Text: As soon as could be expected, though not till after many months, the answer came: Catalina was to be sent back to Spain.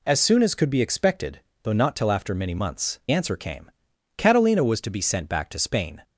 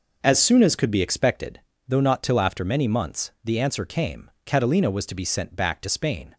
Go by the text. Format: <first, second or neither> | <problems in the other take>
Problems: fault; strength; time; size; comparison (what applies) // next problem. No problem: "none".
second | skips "the"; at 3.0 s